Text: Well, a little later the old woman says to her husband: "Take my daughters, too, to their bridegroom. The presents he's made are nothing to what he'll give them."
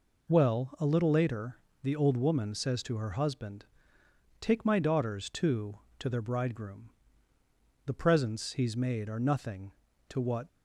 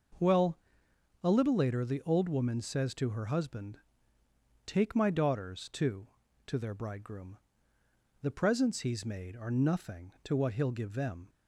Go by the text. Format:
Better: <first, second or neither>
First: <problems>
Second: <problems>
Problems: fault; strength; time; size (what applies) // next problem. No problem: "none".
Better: second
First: pauses between "later" and "the"; slight; at 1.5 s; 0.26 s long // stops before "he'll give them"; at 10.4 s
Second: none